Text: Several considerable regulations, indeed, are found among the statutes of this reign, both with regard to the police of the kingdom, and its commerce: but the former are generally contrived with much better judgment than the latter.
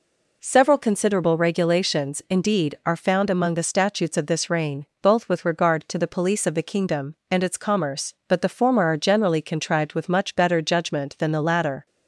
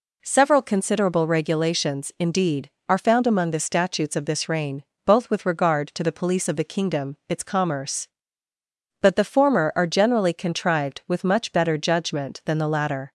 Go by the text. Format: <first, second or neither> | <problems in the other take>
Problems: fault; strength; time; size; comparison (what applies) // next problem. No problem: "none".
first | skips "and"; at 7.2 s